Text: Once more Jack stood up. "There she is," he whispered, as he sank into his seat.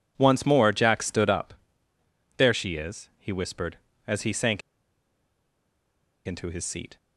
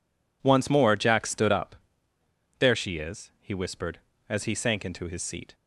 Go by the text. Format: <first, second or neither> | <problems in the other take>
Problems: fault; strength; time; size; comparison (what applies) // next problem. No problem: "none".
second | pauses between "sank" and "into"; strong; at 4.6 s; 1.6 s long